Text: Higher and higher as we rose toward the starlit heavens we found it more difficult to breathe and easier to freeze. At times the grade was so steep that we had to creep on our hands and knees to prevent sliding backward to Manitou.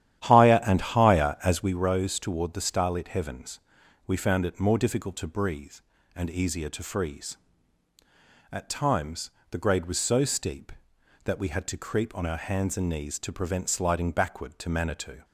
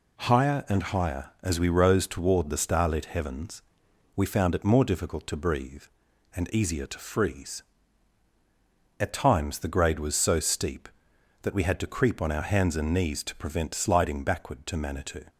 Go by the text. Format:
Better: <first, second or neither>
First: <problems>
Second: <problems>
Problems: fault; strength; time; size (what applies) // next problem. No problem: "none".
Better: second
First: starts louder than the rest; strong; until 1.7 s; 11.5 dB // pauses between "heavens" and "we"; noticeable; at 3.5 s; 0.48 s long // pauses between "times" and "the"; slight; at 9.2 s; 0.20 s long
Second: pauses between "heavens" and "we"; noticeable; at 3.6 s; 0.54 s long